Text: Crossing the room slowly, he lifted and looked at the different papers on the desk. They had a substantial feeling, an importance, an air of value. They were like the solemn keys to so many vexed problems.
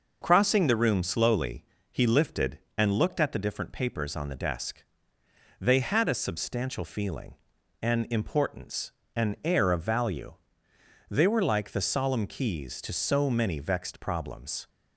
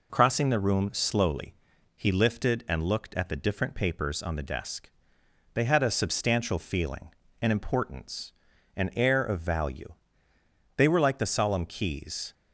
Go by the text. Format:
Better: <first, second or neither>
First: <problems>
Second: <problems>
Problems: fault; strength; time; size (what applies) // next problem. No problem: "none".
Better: first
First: none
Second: stops before "to so many vexed problems"; at 12.3 s